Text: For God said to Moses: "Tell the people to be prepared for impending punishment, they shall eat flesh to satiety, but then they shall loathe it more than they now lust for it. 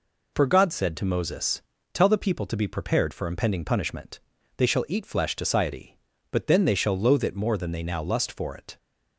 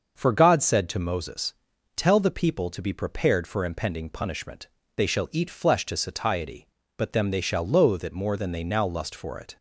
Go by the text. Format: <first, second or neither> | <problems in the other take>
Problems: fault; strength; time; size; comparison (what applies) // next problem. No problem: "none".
first | starts louder than the rest; until 1.1 s; 6.5 dB // says "them" for "then"; at 7.1 s